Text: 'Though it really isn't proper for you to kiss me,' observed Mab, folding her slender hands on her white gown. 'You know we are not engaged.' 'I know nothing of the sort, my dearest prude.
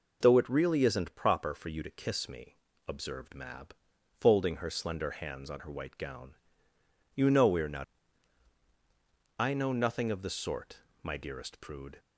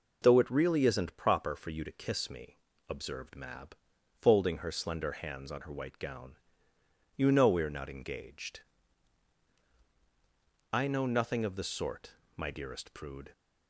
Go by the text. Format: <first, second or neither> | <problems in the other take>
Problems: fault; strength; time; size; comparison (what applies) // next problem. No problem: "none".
second | skips "engaged"; at 8.6 s